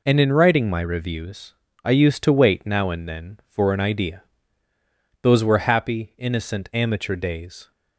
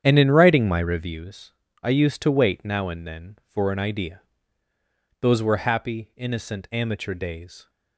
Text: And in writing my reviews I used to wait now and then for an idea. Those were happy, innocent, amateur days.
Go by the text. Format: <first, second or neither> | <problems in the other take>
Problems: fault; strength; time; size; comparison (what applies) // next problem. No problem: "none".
first | starts louder than the rest; strong; until 1.1 s; 8.5 dB // pauses between "reviews" and "I"; slight; at 1.5 s; 0.32 s long; slight in the first